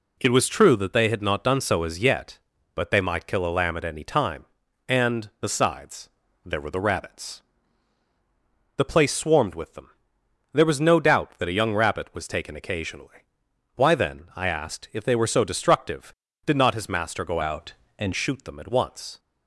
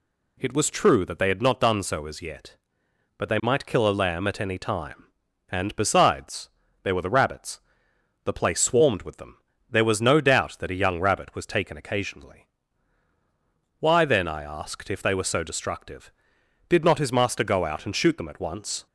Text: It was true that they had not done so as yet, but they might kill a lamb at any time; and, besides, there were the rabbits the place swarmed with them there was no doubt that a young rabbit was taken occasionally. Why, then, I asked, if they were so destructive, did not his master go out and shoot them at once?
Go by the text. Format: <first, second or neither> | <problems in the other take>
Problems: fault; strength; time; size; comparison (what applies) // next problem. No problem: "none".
second | pauses between "rabbits" and "the"; strong; at 7.4 s; 1.3 s long; noticeable in the second // pauses between "them" and "there"; noticeable; at 9.8 s; 0.62 s long; slight in the second // changes voice from "out" to "and"; from 17.4 to 18.1 s; 0.7 s long